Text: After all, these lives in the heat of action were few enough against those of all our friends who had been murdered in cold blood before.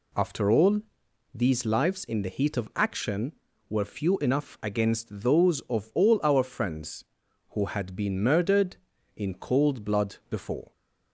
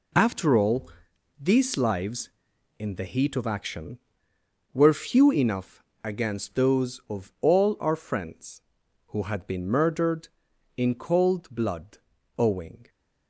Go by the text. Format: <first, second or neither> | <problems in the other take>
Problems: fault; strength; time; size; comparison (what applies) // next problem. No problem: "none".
first | pauses between "enough" and "against"; slight; at 5.8 s; 0.20 s long // says "owing" for "before"; at 12.3 s